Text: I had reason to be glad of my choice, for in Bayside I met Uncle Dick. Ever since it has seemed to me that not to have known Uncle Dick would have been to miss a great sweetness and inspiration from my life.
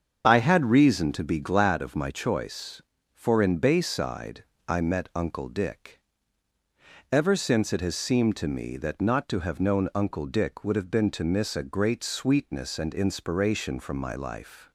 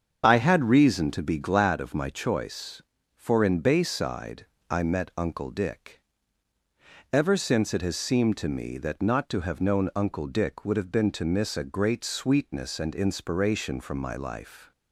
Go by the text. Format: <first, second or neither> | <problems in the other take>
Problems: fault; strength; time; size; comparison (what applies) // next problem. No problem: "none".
neither | starts louder than the rest; the same in both // pauses between "Bayside" and "I"; slight; the same in both